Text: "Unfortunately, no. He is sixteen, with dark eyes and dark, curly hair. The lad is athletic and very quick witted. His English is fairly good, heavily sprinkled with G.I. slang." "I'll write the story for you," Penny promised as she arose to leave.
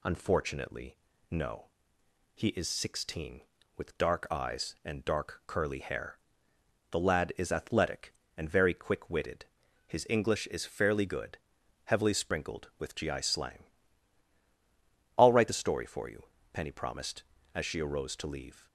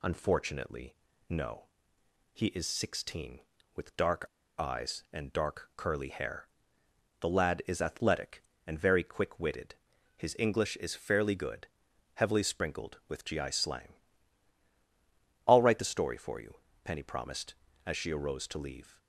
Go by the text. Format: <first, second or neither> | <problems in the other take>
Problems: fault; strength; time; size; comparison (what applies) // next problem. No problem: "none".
first | pauses between "dark" and "eyes"; slight; at 4.2 s; 0.33 s long